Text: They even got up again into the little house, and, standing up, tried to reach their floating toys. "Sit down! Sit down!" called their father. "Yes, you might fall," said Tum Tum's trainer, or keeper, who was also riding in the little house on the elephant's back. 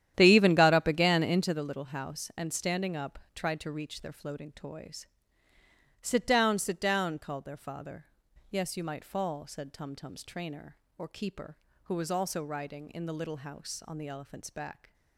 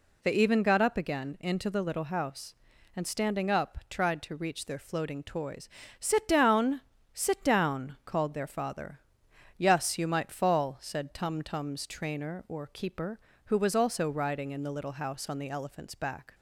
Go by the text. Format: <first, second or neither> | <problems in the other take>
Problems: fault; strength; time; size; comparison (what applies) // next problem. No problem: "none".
second | starts louder than the rest; strong; until 1.5 s; 11 dB